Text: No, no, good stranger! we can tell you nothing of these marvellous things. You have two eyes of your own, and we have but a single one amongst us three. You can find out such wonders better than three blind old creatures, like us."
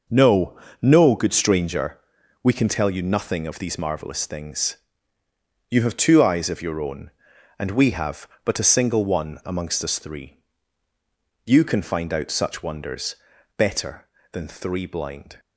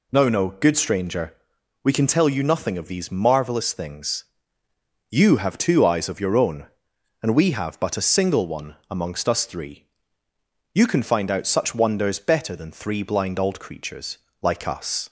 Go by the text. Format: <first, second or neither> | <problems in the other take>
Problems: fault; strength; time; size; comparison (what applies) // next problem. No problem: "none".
second | pauses between "wonders" and "better"; at 13.1 s; 0.42 s long // stops before "old creatures like us"; at 15.3 s